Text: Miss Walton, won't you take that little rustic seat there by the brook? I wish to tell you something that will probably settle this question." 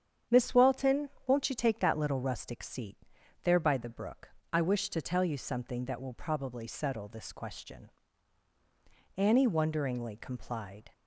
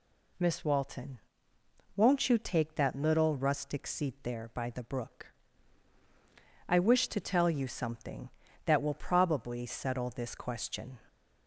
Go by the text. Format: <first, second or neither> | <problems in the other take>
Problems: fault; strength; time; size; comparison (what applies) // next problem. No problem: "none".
second | starts louder than the rest; strong; until 1.4 s; 8.5 dB // pauses between "seat" and "there"; noticeable; at 2.9 s; 0.46 s long // goes on to say "Annie wonderingly complied"; strong; from 9.1 s on; 1.7 s long